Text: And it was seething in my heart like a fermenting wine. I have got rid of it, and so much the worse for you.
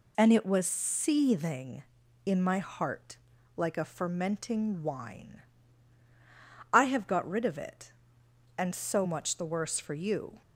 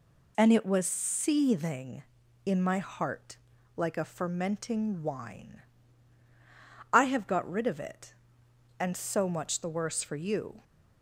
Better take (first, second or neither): neither